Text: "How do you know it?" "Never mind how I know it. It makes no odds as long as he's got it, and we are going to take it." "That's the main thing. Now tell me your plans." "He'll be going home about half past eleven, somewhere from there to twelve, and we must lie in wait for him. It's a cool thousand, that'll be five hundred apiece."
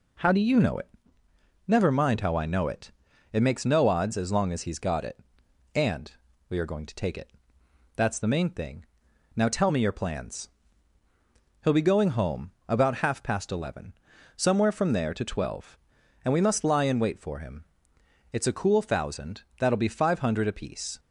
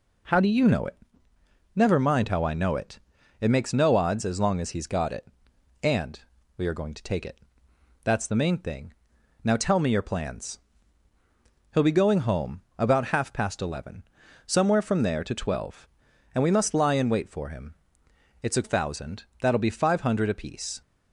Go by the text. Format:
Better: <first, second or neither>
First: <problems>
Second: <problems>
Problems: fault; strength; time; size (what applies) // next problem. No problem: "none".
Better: first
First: pauses between "and" and "we"; at 6.0 s; 0.40 s long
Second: pauses between "and" and "we"; at 6.1 s; 0.40 s long // skips "cool"; at 18.6 s